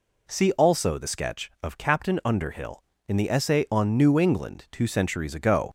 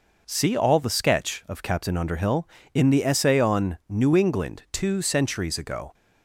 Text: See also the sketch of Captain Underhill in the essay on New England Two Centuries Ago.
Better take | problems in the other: first | says "all" for "also"; at 0.5 s

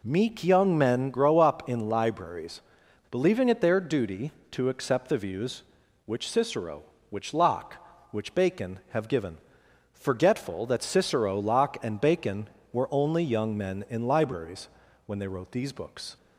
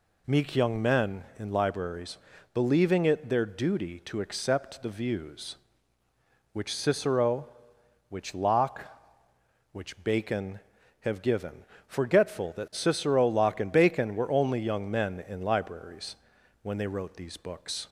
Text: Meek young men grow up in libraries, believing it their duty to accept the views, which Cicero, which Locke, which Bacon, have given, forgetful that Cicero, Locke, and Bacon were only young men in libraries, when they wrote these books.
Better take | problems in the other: first | skips "grow up"; at 1.3 s

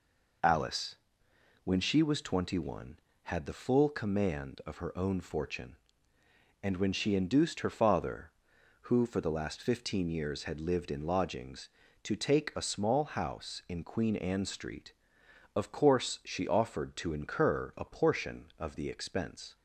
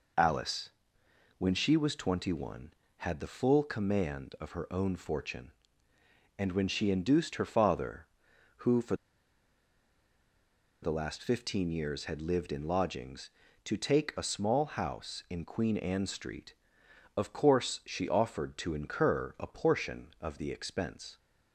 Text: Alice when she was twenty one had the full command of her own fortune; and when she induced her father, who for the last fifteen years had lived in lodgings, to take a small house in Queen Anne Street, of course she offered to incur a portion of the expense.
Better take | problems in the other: first | pauses between "Alice" and "when"; noticeable; at 0.7 s; 0.68 s long; noticeable in the first // pauses between "for" and "the"; strong; at 8.9 s; 1.8 s long

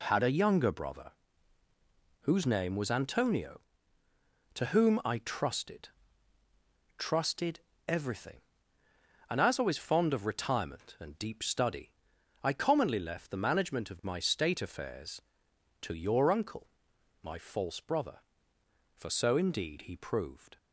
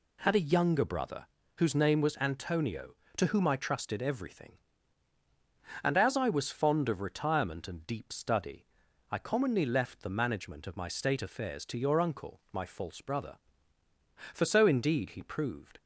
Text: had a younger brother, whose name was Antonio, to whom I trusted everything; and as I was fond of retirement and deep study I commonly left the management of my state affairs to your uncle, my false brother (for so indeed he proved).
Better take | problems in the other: second | says "trusted" twice; at 6.9 s // pauses between "study" and "I"; noticeable; at 11.9 s; 0.50 s long; noticeable in the second

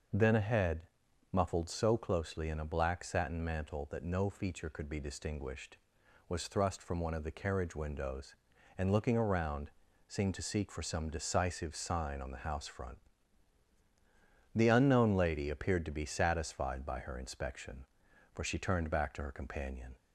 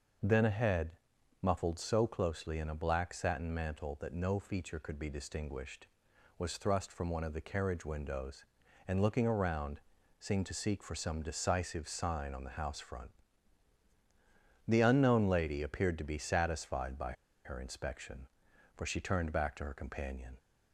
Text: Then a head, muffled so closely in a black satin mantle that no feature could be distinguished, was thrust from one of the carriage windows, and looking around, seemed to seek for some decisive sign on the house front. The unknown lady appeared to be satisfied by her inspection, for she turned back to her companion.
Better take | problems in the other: first | pauses between "by" and "her"; slight; at 17.1 s; 0.31 s long

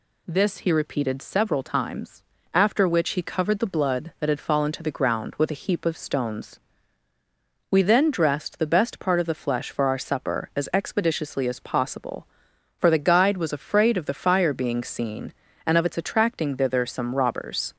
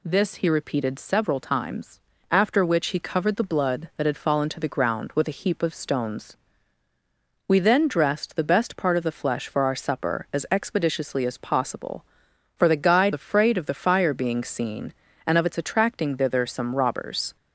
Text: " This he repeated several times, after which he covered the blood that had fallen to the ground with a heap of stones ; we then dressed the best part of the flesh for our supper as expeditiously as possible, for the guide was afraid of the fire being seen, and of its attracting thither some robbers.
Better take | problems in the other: first | skips "was"; at 13.1 s

